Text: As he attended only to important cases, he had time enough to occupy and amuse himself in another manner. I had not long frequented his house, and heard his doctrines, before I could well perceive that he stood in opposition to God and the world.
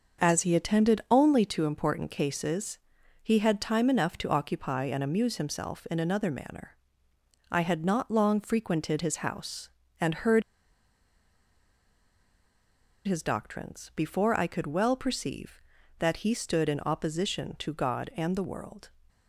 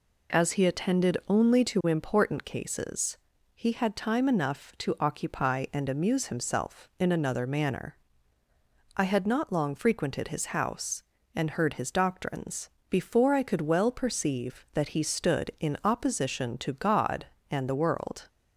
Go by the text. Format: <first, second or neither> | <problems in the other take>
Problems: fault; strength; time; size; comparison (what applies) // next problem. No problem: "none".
second | starts louder than the rest; until 1.3 s; 6.5 dB // pauses between "heard" and "his"; strong; at 10.4 s; 2.6 s long